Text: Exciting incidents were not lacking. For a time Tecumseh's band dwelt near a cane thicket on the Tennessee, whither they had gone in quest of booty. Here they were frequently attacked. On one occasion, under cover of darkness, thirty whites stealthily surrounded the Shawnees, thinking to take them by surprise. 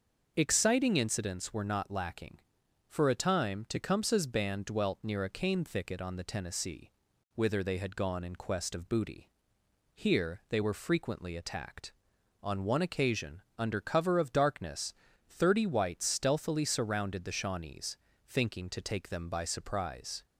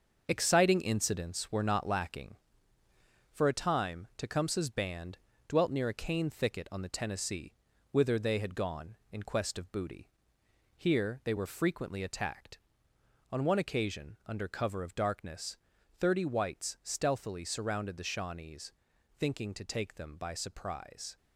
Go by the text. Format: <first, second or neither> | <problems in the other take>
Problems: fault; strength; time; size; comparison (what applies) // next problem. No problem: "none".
first | gets quieter; throughout; 6.5 dB // starts louder than the rest; until 1.3 s; 6.5 dB; also in the first // pauses between "band" and "dwelt"; slight; at 5.1 s; 0.30 s long